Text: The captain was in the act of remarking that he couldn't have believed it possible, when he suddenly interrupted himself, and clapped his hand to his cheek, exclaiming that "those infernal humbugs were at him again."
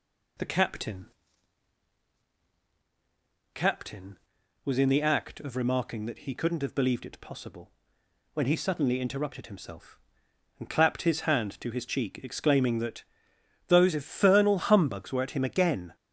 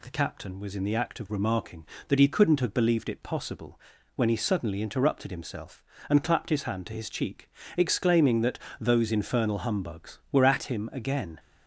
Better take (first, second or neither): second